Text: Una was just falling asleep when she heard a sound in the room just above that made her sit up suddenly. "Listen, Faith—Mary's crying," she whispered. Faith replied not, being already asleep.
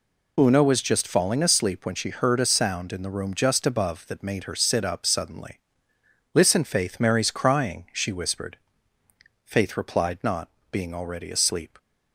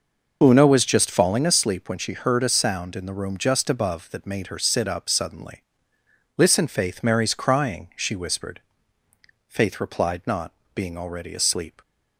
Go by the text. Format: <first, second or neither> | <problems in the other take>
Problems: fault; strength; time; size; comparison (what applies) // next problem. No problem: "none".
first | starts louder than the rest; noticeable; until 1.5 s; 5.5 dB